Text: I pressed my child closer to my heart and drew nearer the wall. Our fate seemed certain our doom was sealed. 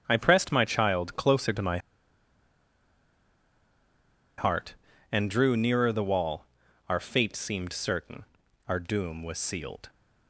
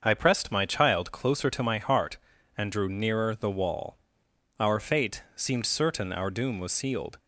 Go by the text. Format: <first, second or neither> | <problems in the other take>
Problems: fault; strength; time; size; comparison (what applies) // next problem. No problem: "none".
second | starts louder than the rest; strong; until 1.0 s; 8 dB; also in the second // pauses between "my" and "heart"; strong; at 1.7 s; 2.5 s long // pauses between "certain" and "our"; at 8.2 s; 0.44 s long